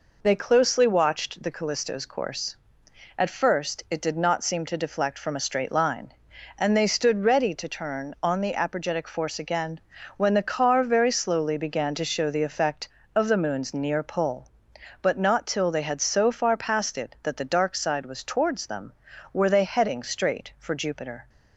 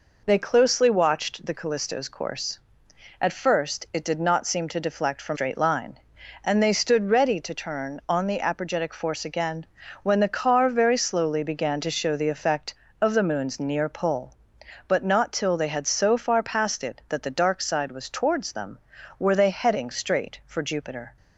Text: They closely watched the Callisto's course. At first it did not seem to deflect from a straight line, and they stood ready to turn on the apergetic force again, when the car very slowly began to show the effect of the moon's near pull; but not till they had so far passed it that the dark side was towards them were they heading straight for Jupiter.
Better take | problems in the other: first | skips "a"; at 5.3 s

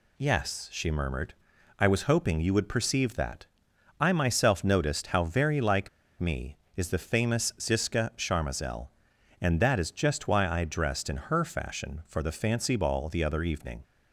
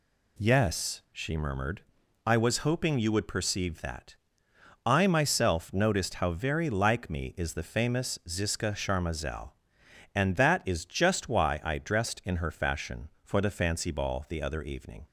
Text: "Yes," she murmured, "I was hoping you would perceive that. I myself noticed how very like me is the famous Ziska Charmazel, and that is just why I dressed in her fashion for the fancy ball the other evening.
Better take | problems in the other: second | pauses between "like" and "me"; slight; at 5.8 s; 0.30 s long

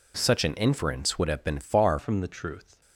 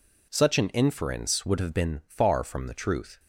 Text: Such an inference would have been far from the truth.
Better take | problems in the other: second | changes voice at "from"; from 1.9 s on; 0.9 s long

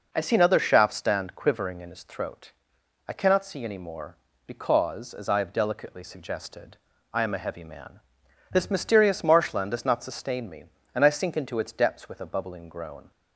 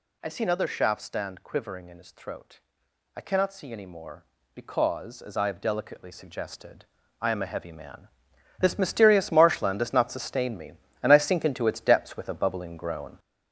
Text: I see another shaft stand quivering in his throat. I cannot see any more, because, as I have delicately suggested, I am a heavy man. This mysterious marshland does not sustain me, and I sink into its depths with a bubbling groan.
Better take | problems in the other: first | gets louder; throughout; 6.5 dB

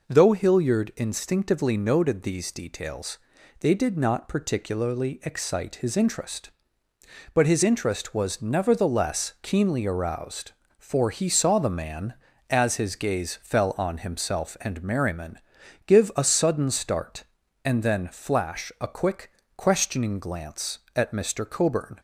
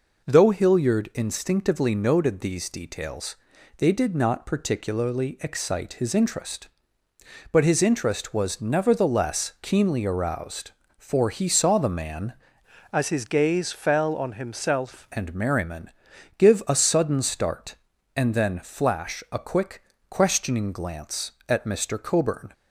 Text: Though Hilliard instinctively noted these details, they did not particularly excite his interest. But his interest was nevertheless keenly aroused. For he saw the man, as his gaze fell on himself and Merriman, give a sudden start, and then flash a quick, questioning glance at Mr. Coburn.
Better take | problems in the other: first | changes voice from "as" to "himself"; from 12.9 to 15.0 s; 2.1 s long

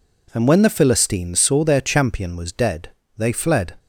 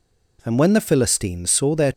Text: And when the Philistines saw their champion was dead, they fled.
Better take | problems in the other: first | stops before "champion was dead they fled"; at 1.9 s

